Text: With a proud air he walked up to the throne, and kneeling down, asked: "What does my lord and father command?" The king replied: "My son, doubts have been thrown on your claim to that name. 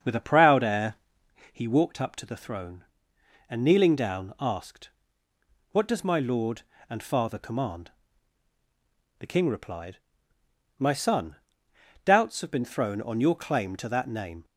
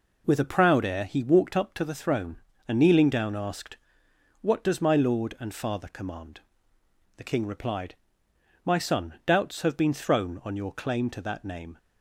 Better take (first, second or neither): second